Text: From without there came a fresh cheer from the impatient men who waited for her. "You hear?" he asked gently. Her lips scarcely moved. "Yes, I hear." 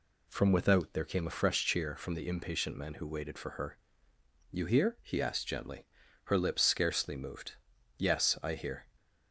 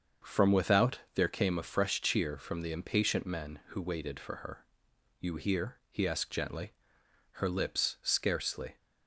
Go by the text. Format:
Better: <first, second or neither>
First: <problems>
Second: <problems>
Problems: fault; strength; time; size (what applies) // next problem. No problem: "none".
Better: first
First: none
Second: starts louder than the rest; until 1.3 s; 6.5 dB // pauses between "without" and "there"; slight; at 0.9 s; 0.16 s long // stops before "moved Yes I hear"; at 8.7 s